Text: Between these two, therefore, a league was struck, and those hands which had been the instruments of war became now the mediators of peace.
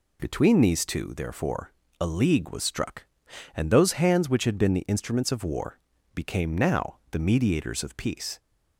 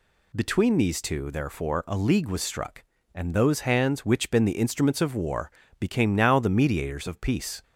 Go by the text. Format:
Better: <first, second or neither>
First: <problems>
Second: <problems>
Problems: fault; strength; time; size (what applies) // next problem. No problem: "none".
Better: first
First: pauses between "war" and "became"; slight; at 5.7 s; 0.34 s long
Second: skips "had"; at 4.3 s // pauses between "war" and "became"; slight; at 5.5 s; 0.28 s long